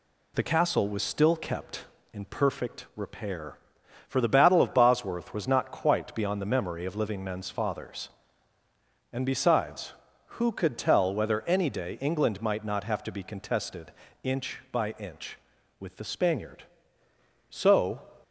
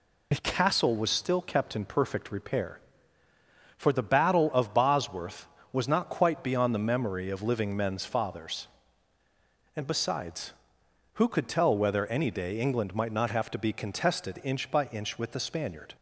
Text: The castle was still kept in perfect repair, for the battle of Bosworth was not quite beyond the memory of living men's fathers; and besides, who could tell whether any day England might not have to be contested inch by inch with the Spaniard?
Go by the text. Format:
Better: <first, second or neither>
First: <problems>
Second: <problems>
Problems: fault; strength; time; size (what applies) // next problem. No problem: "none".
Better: second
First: pauses between "contested" and "inch"; slight; at 13.9 s; 0.32 s long // goes on to say "So"; from 17.4 s on; 0.52 s long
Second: none